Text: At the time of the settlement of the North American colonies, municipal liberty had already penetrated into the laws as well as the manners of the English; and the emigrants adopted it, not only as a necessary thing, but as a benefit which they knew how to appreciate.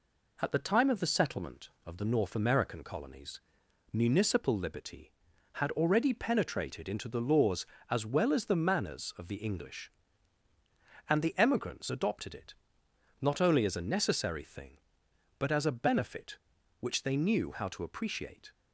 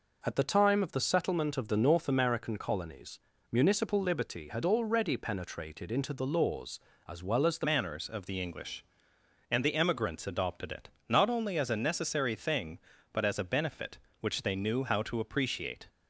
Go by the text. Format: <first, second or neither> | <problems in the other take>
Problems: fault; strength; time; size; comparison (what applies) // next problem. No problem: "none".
first | changes voice at "manners"; from 7.6 s on; 8.2 s long